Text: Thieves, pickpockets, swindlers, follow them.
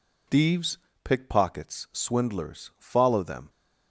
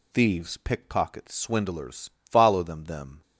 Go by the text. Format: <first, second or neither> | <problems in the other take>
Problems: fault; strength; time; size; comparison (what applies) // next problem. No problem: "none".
first | says "them" twice; at 2.8 s